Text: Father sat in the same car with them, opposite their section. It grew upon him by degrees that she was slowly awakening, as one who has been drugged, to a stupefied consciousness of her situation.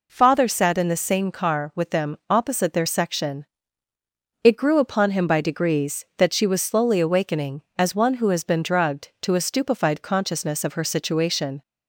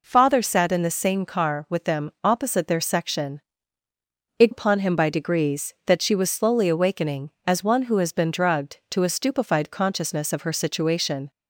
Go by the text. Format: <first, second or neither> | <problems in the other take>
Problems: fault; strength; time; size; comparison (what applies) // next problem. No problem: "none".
first | skips "grew"; at 4.5 s